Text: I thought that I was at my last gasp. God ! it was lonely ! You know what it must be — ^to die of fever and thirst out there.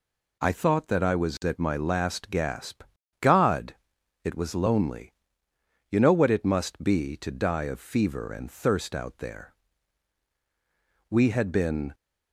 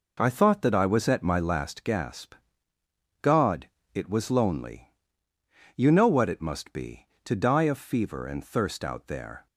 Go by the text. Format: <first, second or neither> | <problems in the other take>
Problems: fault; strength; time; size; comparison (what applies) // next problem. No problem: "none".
second | goes on to say "We had been"; noticeable; from 11.0 s on; 0.84 s long